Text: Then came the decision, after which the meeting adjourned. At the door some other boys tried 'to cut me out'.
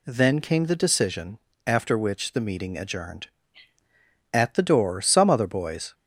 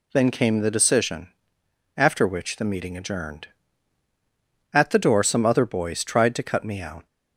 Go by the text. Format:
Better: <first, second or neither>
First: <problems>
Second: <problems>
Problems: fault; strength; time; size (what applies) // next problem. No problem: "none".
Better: second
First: stops before "tried to cut me out"; at 5.9 s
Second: none